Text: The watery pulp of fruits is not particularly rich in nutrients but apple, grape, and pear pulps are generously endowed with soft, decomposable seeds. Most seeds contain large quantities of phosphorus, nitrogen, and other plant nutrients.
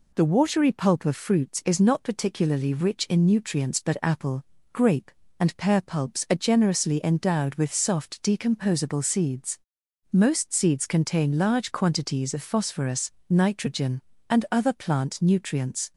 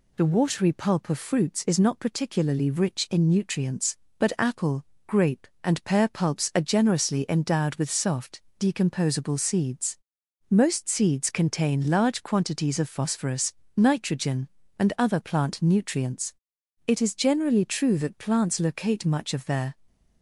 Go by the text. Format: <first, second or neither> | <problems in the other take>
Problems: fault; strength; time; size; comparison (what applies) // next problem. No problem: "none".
first | goes on to say "It is generally true that plants locate much of their"; strong; from 16.8 s on; 2.8 s long